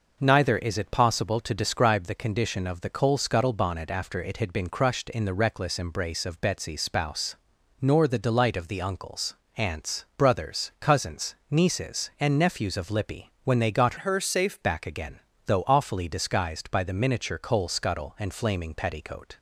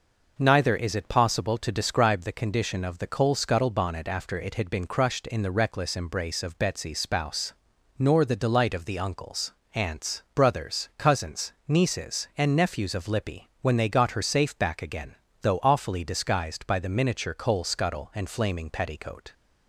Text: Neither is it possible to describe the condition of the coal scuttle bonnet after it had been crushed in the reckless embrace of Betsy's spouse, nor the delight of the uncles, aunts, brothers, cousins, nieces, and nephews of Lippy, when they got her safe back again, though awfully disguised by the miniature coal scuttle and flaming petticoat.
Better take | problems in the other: second | changes voice from "her" to "safe"; from 13.9 to 14.5 s; 0.6 s long

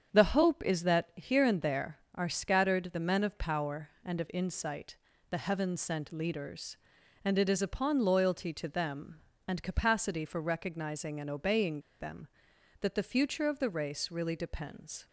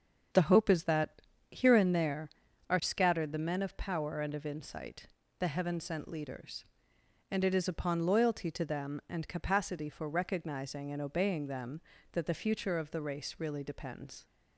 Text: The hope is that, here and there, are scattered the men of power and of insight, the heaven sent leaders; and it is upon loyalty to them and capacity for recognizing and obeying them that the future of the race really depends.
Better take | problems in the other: second | starts louder than the rest; strong; until 1.2 s; 7.5 dB; also in the second // pauses between "obeying" and "them"; slight; at 11.8 s; 0.17 s long

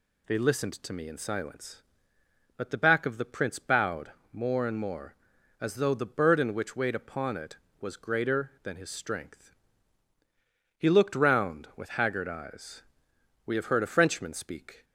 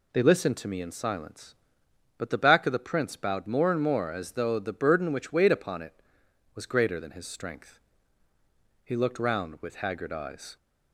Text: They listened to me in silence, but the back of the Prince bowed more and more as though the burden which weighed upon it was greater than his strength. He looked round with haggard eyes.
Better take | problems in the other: second | pauses between "bowed" and "more"; slight; at 4.1 s; 0.20 s long // goes on to say "We have heard a Frenchman speak"; from 13.4 s on; 1.3 s long

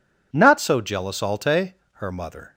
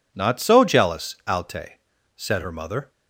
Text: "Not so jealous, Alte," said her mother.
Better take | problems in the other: second | skips "said"; at 1.8 s

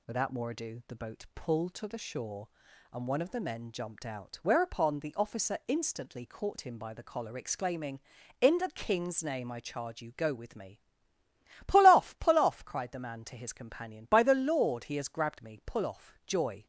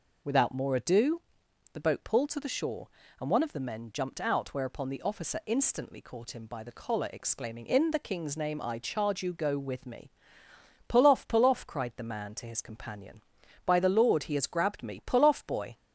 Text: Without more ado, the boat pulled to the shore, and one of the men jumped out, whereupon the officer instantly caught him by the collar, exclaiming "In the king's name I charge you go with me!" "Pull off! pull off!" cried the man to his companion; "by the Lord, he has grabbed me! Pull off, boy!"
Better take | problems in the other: second | says "joy" for "boy"; at 16.2 s

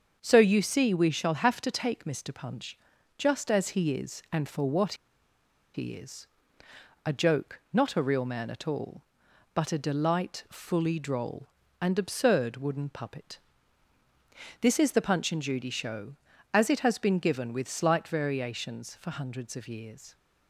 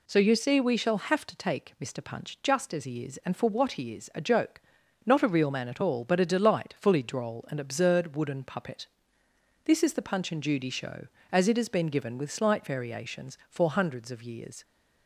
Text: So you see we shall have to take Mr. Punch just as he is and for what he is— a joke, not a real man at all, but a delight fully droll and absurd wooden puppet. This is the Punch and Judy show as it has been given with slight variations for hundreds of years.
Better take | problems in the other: second | starts louder than the rest; until 1.2 s; 7 dB // pauses between "Punch" and "just"; at 2.7 s; 0.40 s long // pauses between "what" and "he"; noticeable; at 4.9 s; 0.80 s long

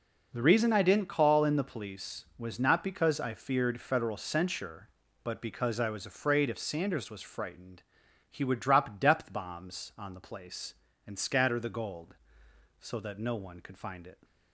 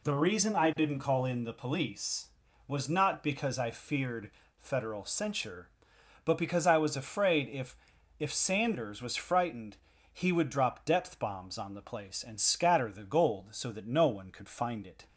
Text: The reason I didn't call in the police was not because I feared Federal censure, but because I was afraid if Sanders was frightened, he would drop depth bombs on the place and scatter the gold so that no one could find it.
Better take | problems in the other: first | pauses between "feared" and "Federal"; slight; at 4.2 s; 0.26 s long // says "if" twice; at 8.1 s

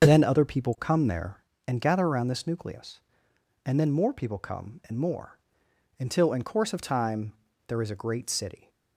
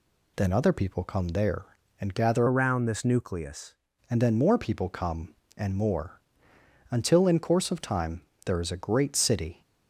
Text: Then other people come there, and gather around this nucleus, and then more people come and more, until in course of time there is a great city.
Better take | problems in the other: first | changes voice from "around" to "nucleus"; from 2.4 to 3.7 s; 1.3 s long // pauses between "time" and "there"; slight; at 8.2 s; 0.26 s long; slight in the first

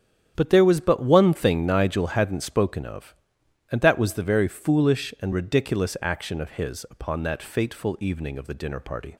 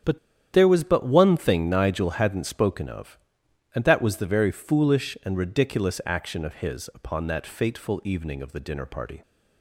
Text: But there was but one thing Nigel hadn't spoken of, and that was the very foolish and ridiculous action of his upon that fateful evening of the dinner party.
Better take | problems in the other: first | starts louder than the rest; strong; until 1.4 s; 9 dB; strong in the first // pauses between "But" and "there"; slight; at 0.1 s; 0.34 s long

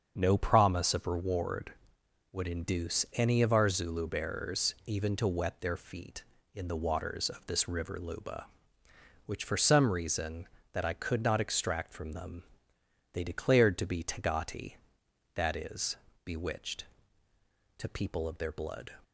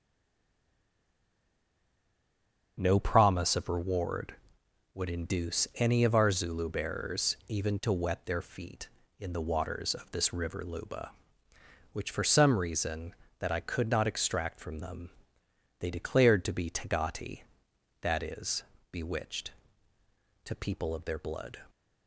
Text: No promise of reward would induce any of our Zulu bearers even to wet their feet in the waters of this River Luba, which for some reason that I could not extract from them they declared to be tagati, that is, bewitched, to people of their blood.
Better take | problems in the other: first | stays silent before the first word; strong; until 2.7 s; 2.7 s long // starts louder than the rest; until 3.8 s; 6.5 dB; also in the first // pauses between "them" and "they"; noticeable; at 15.1 s; 0.66 s long; noticeable in the first

